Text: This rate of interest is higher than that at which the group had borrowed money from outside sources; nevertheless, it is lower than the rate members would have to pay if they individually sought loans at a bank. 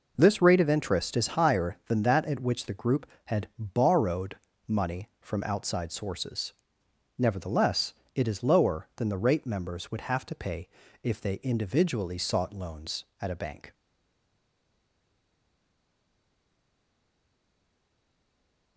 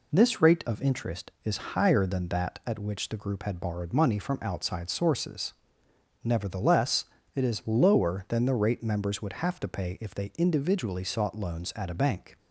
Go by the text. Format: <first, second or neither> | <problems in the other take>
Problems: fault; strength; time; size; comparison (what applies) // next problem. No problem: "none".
second | pauses between "borrowed" and "money"; slight; at 4.3 s; 0.28 s long // pauses between "pay" and "if"; slight; at 10.6 s; 0.34 s long // stays silent after the last word; strong; from 13.7 s on; 5.0 s long